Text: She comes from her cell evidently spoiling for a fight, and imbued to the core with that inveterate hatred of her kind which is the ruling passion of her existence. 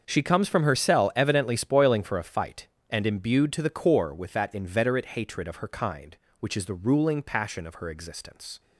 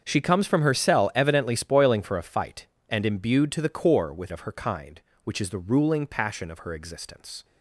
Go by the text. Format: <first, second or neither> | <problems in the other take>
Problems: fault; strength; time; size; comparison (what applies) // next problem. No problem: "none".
first | starts louder than the rest; strong; until 1.0 s; 7 dB; also in the first // skips "that inveterate hatred"; at 4.3 s